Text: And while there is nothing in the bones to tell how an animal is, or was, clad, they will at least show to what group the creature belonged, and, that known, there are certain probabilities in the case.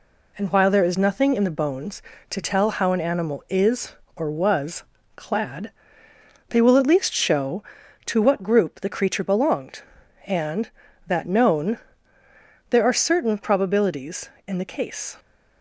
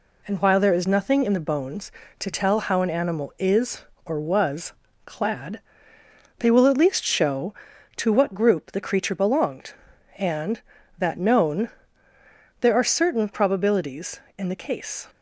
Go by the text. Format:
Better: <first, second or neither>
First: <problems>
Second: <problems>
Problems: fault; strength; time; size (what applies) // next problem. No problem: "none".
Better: neither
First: none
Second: none